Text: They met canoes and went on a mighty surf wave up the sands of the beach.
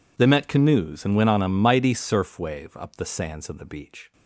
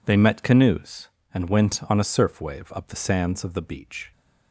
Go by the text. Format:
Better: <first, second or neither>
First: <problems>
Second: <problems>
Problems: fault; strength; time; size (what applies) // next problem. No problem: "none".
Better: first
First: none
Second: skips "mighty"; at 2.0 s